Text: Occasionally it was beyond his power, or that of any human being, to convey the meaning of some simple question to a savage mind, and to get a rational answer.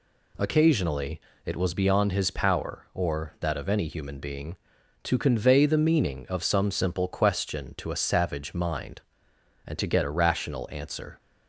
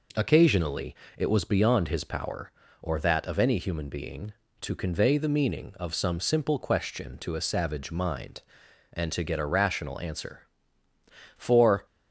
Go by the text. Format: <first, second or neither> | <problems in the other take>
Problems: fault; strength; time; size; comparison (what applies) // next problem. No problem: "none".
first | pauses between "Occasionally" and "it"; slight; at 0.9 s; 0.22 s long; slight in the first // goes on to say "For"; slight; from 11.3 s on; 0.48 s long